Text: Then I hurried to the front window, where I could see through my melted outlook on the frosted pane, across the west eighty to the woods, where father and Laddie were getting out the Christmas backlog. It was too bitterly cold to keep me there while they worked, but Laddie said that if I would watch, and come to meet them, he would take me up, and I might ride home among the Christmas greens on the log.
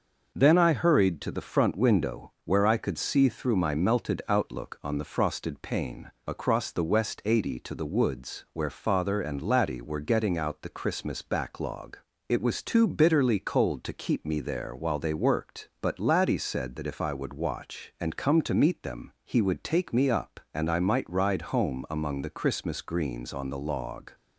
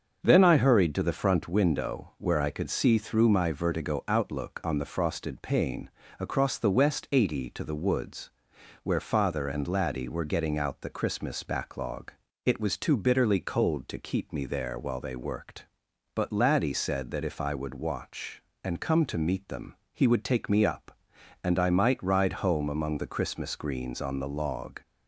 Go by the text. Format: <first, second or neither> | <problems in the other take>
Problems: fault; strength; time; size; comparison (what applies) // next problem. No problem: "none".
first | starts louder than the rest; until 1.2 s; 6.5 dB; noticeable in the first // says "vertigo" for "melted"; at 3.5 s